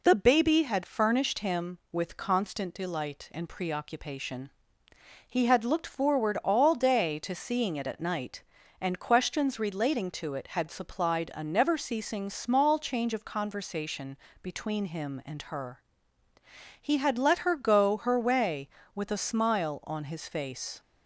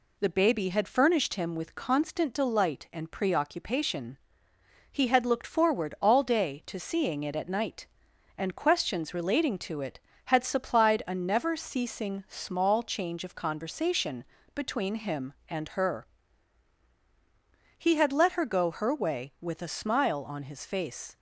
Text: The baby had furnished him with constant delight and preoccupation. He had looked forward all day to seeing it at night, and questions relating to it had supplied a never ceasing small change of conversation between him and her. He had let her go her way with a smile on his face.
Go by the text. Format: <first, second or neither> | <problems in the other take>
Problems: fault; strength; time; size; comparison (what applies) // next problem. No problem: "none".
neither | pauses between "conversation" and "between"; slight; the same in both